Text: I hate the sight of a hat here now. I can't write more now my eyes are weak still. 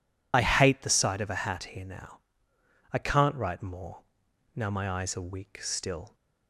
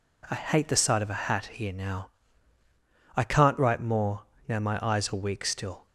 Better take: second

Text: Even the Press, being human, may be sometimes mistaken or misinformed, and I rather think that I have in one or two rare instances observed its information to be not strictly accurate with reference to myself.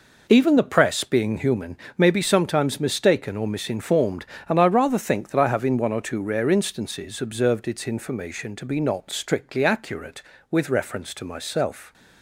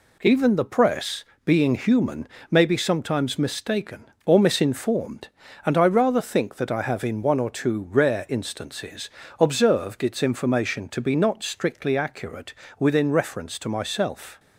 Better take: first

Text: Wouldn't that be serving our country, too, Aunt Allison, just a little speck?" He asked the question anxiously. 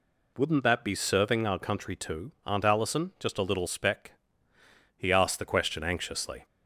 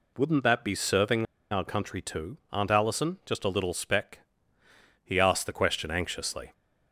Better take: first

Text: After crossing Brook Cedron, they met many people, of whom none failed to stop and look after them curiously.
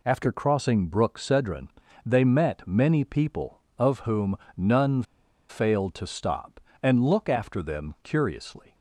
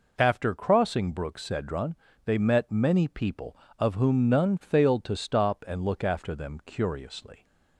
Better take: second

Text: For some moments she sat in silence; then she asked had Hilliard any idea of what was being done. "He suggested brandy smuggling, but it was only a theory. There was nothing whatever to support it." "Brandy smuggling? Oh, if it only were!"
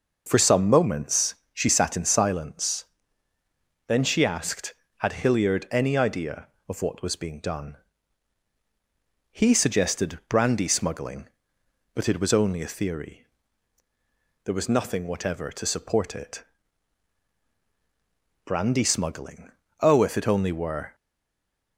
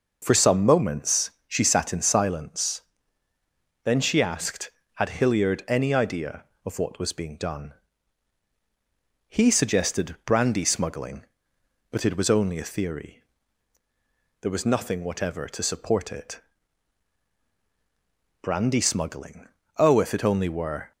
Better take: second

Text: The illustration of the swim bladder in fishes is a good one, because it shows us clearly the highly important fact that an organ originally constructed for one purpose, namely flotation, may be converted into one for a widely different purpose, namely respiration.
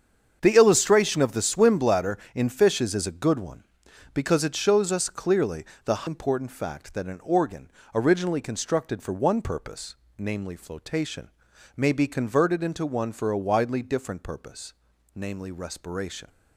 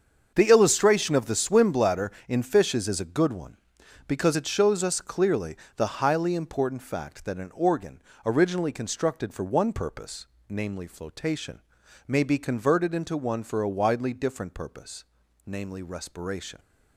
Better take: second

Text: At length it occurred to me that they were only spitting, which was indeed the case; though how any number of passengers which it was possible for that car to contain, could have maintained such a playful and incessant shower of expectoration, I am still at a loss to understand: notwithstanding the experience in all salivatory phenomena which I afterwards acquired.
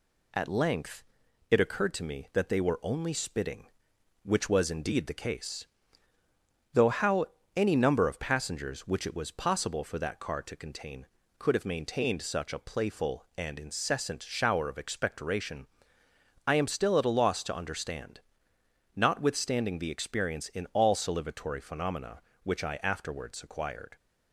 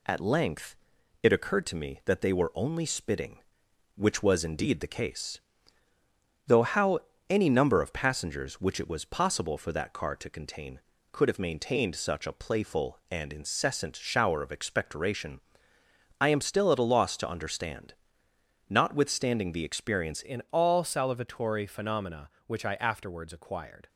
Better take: first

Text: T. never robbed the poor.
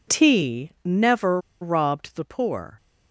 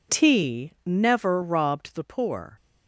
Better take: second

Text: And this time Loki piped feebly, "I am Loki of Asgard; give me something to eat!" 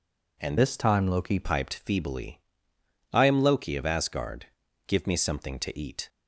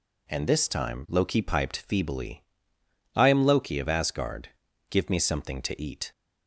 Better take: second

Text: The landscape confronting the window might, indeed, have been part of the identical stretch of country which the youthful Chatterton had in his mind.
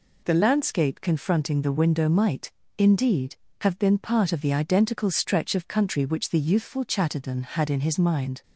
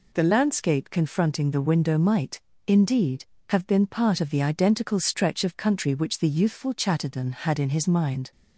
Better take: neither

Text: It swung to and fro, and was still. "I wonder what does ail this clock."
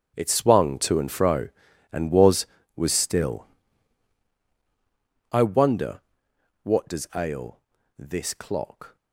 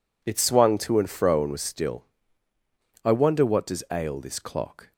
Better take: second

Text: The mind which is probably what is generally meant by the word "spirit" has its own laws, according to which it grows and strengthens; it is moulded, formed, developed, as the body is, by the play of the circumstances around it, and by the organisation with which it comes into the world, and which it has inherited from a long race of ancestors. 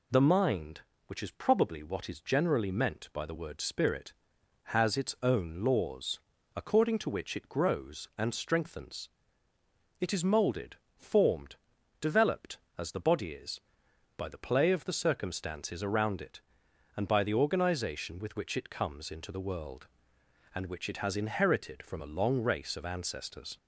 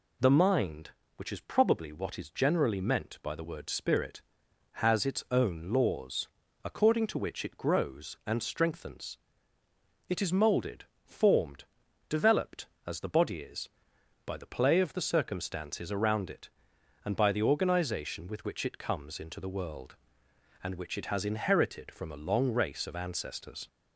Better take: neither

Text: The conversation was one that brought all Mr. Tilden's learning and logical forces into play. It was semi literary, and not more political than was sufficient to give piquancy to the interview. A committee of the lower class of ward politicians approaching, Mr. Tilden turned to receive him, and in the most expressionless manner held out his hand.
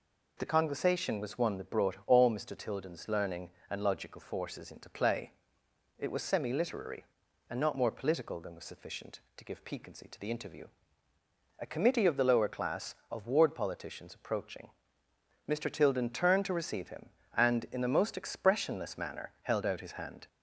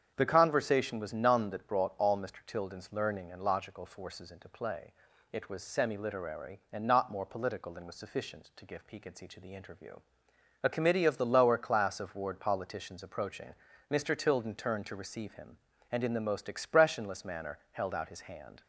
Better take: first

